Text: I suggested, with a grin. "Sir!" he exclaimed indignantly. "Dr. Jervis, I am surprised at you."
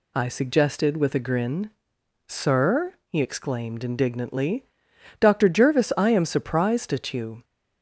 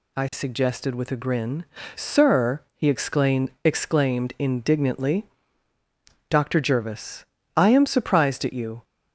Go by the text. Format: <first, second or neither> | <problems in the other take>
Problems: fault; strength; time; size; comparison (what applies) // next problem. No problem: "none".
first | says "exclaimed" twice; at 3.6 s